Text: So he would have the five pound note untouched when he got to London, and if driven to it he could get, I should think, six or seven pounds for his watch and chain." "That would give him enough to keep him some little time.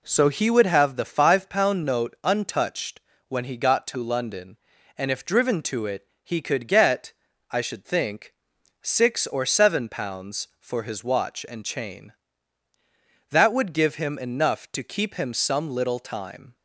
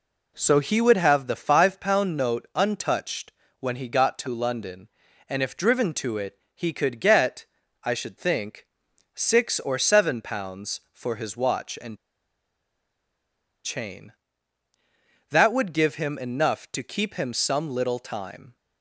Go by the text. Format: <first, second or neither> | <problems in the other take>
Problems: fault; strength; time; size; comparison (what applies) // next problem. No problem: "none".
first | pauses between "untouched" and "when"; slight; at 3.3 s; 0.30 s long; slight in the first // pauses between "it" and "he"; slight; at 6.3 s; 0.16 s long; slight in the first // pauses between "and" and "chain"; strong; at 11.9 s; 1.6 s long